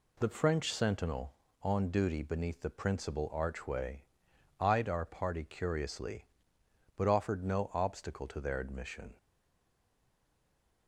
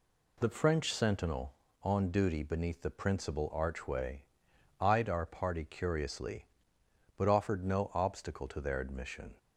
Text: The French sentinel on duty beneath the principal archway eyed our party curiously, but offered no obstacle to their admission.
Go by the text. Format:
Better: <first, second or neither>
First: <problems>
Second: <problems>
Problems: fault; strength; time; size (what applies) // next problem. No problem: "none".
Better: second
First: pauses between "archway" and "eyed"; noticeable; at 4.0 s; 0.56 s long // stays silent after the last word; noticeable; from 9.1 s on; 1.7 s long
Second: pauses between "archway" and "eyed"; noticeable; at 4.2 s; 0.56 s long